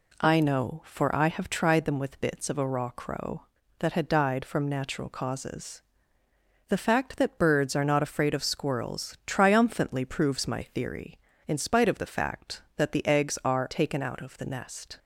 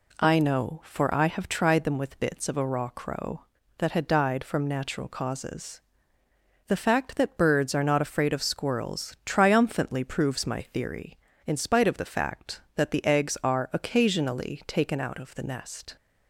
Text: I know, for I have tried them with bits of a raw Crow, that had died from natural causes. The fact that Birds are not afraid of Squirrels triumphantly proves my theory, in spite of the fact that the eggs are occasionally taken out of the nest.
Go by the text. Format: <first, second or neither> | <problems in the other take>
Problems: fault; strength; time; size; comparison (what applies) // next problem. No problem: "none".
second | skips "occasionally"; at 13.7 s